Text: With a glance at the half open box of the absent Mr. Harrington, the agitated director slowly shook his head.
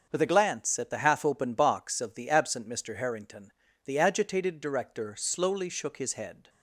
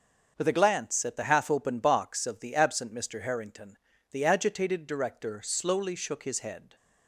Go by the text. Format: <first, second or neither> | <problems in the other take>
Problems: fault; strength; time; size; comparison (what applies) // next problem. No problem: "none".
neither | starts louder than the rest; the same in both